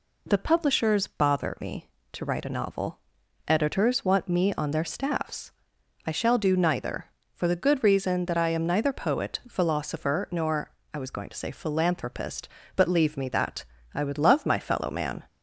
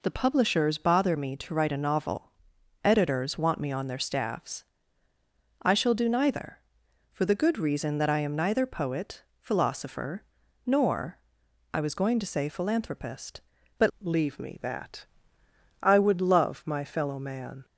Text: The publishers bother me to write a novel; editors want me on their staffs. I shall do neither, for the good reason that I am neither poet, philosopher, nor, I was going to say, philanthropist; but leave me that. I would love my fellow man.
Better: first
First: none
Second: changes voice at "leave"; from 14.0 s on; 3.6 s long

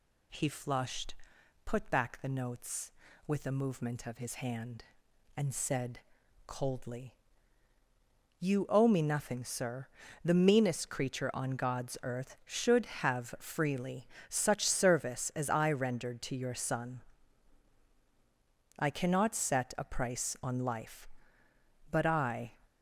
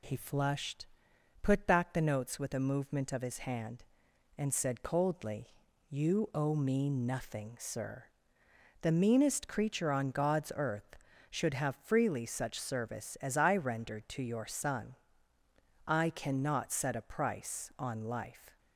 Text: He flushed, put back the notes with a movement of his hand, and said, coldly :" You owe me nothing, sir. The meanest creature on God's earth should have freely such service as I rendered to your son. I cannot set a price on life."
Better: second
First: pauses between "freely" and "such"; slight; at 14.0 s; 0.22 s long // goes on to say "But I"; noticeable; from 21.9 s on; 0.62 s long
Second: none

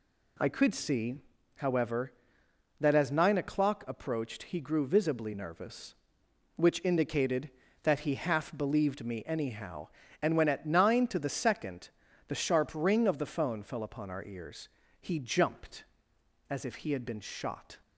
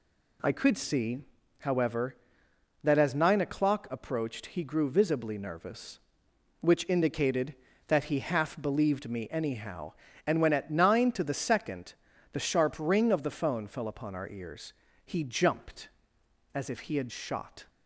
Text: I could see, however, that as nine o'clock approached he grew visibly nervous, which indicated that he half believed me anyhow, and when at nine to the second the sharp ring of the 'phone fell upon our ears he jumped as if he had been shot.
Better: first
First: pauses between "second" and "the"; at 11.8 s; 0.40 s long // pauses between "ears" and "he"; slight; at 14.6 s; 0.32 s long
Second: pauses between "second" and "the"; at 11.9 s; 0.40 s long // pauses between "ears" and "he"; slight; at 14.7 s; 0.32 s long // skips "been"; at 17.0 s

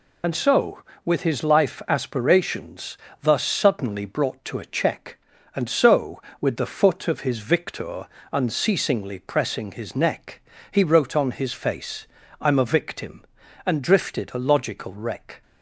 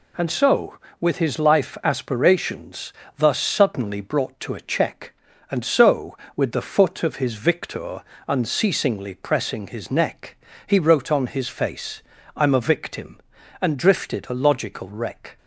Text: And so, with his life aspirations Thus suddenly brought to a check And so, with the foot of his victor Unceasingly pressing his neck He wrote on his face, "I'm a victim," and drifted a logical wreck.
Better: second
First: loses the start of "And"; at 0.2 s; 45 ms // pauses between "aspirations" and "Thus"; slight; at 2.9 s; 0.24 s long // pauses between "victor" and "Unceasingly"; slight; at 8.0 s; 0.26 s long // pauses between "neck" and "He"; slight; at 10.4 s; 0.30 s long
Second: pauses between "aspirations" and "Thus"; slight; at 2.9 s; 0.24 s long // pauses between "victor" and "Unceasingly"; slight; at 8.0 s; 0.26 s long // pauses between "neck" and "He"; slight; at 10.3 s; 0.30 s long

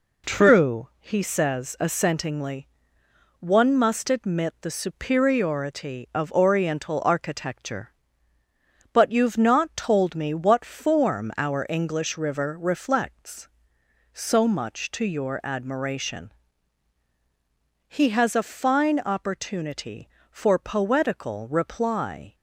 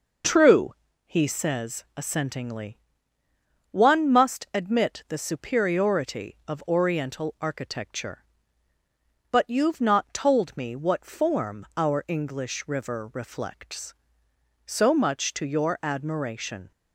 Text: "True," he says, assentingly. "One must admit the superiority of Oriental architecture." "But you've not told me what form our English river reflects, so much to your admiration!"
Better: second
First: goes on to say "He has a fine opportunity for poetical reply"; strong; from 17.8 s on; 4.4 s long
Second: none

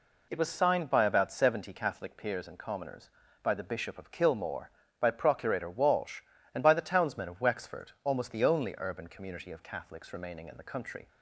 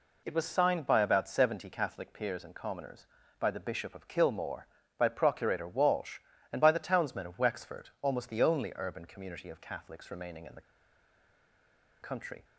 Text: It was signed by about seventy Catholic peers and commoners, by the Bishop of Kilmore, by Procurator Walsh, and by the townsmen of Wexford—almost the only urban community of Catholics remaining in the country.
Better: first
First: none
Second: pauses between "the" and "country"; strong; at 10.6 s; 1.4 s long

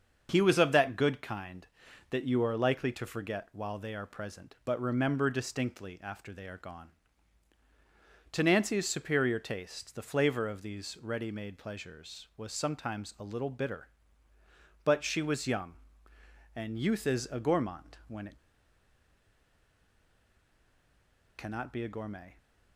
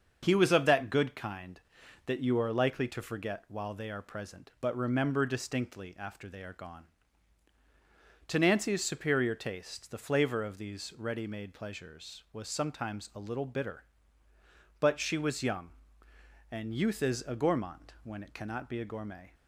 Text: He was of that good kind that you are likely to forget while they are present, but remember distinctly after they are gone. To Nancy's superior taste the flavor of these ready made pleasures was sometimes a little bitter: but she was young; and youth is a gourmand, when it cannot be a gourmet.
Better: second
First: starts louder than the rest; until 1.3 s; 6.5 dB // pauses between "it" and "cannot"; strong; at 18.3 s; 3.0 s long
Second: starts louder than the rest; until 1.2 s; 6.5 dB

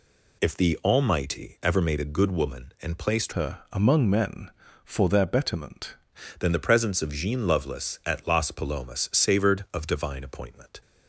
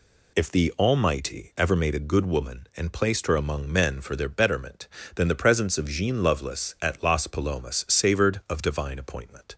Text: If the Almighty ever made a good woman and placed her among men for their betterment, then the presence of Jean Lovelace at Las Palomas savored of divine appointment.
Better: second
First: changes voice from "her" to "betterment"; from 3.3 to 5.9 s; 2.6 s long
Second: none

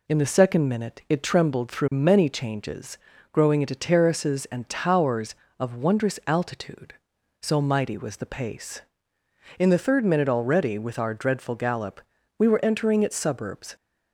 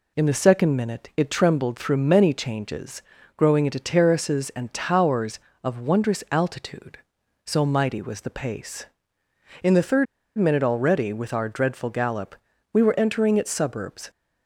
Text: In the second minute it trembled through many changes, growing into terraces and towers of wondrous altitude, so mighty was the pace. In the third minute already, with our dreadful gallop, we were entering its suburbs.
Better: first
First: none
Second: pauses between "third" and "minute"; slight; at 10.0 s; 0.32 s long

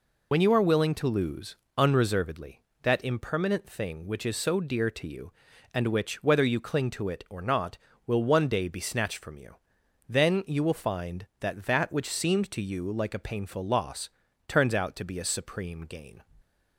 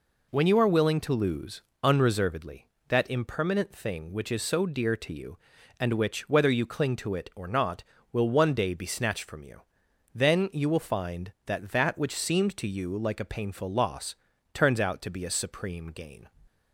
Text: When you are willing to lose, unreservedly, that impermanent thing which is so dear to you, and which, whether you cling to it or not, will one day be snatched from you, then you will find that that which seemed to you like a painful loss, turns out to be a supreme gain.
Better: second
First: loses the start of "When"; at 0.3 s; 65 ms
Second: none

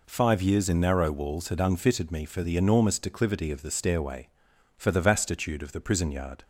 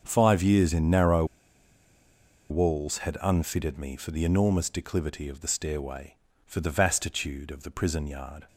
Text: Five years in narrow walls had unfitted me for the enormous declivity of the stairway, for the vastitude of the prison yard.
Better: first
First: none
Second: starts louder than the rest; until 1.0 s; 6.5 dB // pauses between "narrow" and "walls"; strong; at 1.2 s; 1.2 s long

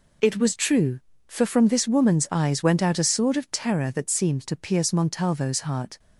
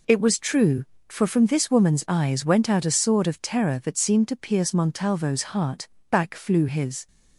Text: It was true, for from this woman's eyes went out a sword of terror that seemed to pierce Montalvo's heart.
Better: first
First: none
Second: goes on to say "Back flew his"; noticeable; from 6.1 s on; 0.96 s long

